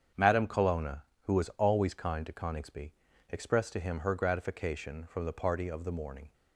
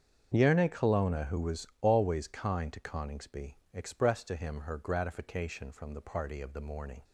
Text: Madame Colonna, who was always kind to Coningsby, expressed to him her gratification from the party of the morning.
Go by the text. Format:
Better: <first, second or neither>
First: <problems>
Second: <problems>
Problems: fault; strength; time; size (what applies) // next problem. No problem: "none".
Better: first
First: starts louder than the rest; strong; until 1.3 s; 7.5 dB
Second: starts louder than the rest; strong; until 1.3 s; 7 dB // says "Yerne" for "Madame"; at 0.3 s // pauses between "was" and "always"; slight; at 1.6 s; 0.16 s long